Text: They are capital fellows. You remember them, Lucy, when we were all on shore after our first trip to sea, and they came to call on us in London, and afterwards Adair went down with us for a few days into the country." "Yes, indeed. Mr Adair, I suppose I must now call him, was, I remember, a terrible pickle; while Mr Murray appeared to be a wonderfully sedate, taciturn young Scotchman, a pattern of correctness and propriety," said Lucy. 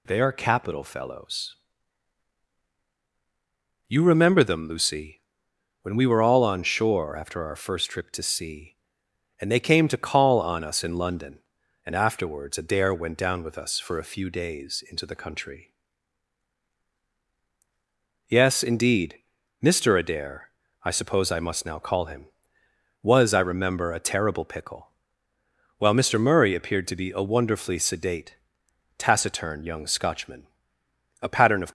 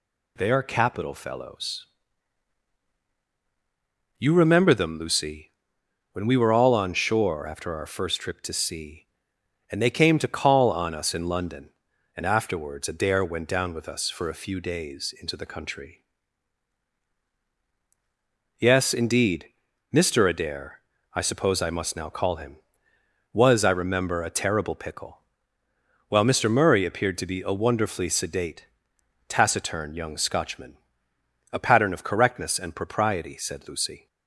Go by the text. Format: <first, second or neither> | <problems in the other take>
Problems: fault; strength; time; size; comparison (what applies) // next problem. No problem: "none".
second | stops before "correctness and propriety said Lucy"; at 31.6 s